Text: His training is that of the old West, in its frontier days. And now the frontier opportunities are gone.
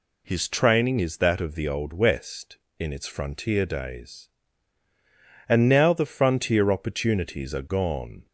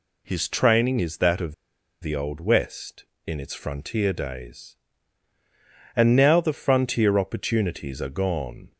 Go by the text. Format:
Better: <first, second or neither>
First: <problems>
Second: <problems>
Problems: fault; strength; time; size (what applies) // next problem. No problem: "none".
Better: first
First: none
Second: pauses between "of" and "the"; noticeable; at 1.5 s; 0.47 s long